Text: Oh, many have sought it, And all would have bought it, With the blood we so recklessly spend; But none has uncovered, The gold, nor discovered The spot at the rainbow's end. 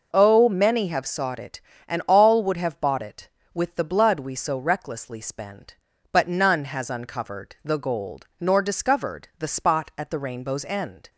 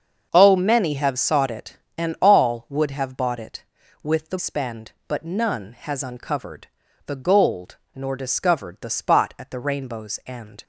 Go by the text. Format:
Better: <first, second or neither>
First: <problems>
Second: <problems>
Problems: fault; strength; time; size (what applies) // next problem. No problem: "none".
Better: first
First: none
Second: starts louder than the rest; until 1.3 s; 6.5 dB // skips "blood we so recklessly"; at 4.3 s